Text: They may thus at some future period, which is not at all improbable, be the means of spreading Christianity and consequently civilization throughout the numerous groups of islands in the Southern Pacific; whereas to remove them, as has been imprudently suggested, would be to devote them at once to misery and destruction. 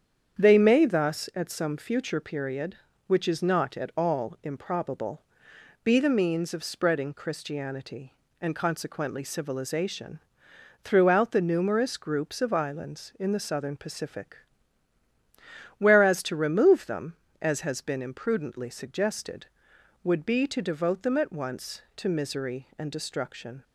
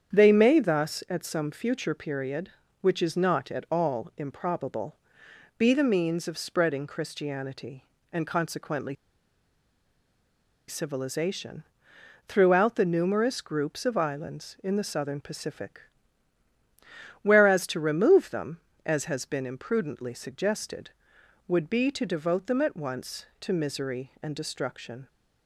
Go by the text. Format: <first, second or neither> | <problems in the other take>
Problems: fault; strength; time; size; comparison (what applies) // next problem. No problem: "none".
first | starts louder than the rest; strong; until 1.1 s; 8 dB; strong in the first // pauses between "consequently" and "civilization"; strong; at 8.9 s; 1.7 s long // pauses between "civilization" and "throughout"; noticeable; at 11.6 s; 0.64 s long; noticeable in the first